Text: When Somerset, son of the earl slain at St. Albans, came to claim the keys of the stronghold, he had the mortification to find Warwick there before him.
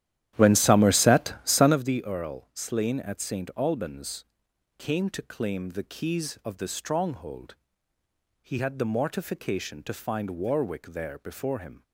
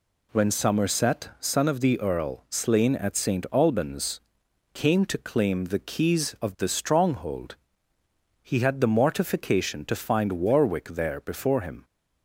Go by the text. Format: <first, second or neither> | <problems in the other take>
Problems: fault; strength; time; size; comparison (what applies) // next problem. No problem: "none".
second | starts louder than the rest; strong; until 1.9 s; 12 dB